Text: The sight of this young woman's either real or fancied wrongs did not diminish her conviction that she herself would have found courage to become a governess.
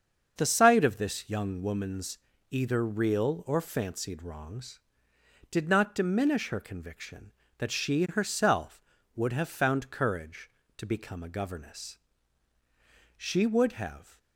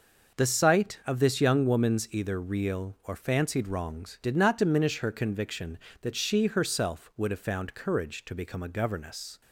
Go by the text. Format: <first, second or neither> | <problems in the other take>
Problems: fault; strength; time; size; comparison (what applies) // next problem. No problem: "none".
second | starts louder than the rest; until 1.3 s; 6.5 dB // pauses between "woman's" and "either"; slight; at 2.1 s; 0.32 s long // goes on to say "She would have"; noticeable; from 13.1 s on; 1.0 s long